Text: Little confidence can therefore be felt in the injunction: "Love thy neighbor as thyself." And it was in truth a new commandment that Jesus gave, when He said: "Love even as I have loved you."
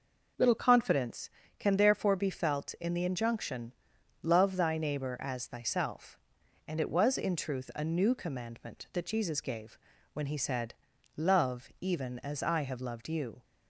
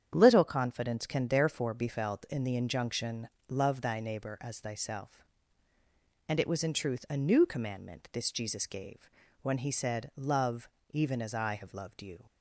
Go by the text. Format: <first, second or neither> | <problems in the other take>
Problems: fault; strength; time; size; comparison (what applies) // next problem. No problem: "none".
first | starts louder than the rest; strong; until 1.1 s; 8.5 dB // says "this" for "that"; at 8.1 s // pauses between "Love" and "even"; slight; at 10.6 s; 0.24 s long